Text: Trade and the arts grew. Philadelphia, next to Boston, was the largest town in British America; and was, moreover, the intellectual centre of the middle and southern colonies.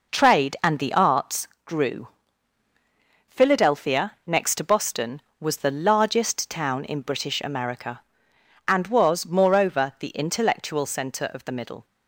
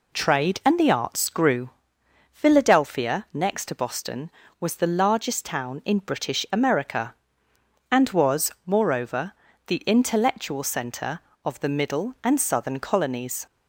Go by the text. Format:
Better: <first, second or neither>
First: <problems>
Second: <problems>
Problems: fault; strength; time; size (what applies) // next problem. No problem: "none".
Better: second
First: pauses between "arts" and "grew"; slight; at 1.4 s; 0.18 s long // stops before "and southern colonies"; at 11.8 s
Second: none